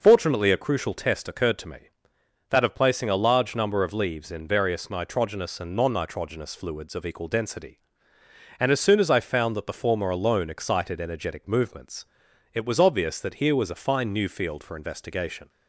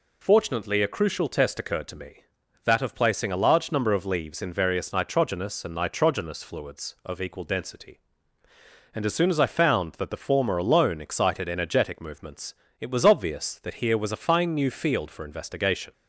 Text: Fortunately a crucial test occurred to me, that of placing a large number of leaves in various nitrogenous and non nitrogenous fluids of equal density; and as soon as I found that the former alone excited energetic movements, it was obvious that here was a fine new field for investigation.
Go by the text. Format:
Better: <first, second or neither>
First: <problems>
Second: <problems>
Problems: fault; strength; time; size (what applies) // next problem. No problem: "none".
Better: first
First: none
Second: skips "non"; at 5.7 s